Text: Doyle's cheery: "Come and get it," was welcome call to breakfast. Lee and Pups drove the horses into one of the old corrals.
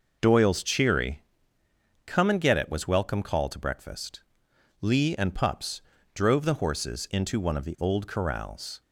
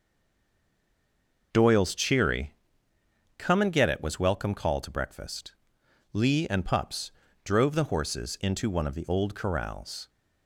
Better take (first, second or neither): first